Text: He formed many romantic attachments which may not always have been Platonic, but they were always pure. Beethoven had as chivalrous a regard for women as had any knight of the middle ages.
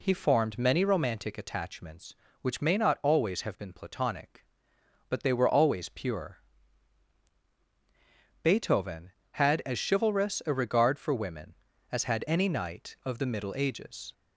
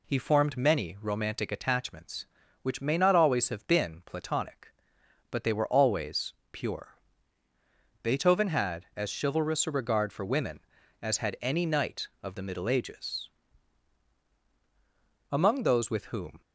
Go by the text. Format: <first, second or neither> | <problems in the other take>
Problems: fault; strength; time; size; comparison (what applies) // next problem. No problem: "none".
first | pauses between "always" and "pure"; slight; at 6.3 s; 0.18 s long // goes on to say "Among those with whom"; noticeable; from 15.2 s on; 1.1 s long